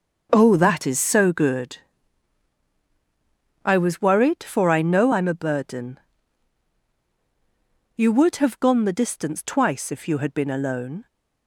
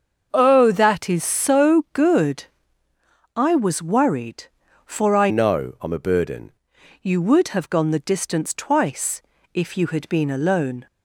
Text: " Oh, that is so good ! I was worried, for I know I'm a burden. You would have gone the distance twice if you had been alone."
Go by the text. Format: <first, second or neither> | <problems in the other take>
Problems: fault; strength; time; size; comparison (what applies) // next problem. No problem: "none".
first | starts louder than the rest; until 1.3 s; 6.5 dB; also in the first // changes voice from "know" to "burden"; from 5.2 to 6.5 s; 1.3 s long // pauses between "twice" and "if"; slight; at 9.2 s; 0.32 s long